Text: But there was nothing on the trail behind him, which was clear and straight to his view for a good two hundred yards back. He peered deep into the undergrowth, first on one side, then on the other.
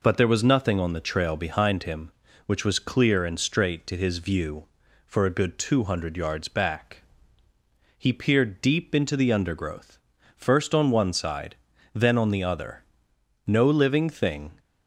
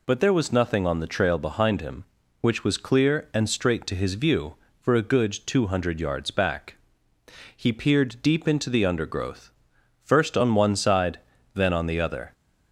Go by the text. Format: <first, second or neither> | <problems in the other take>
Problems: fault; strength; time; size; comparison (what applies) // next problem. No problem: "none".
second | goes on to say "No living thing"; noticeable; from 13.4 s on; 1.1 s long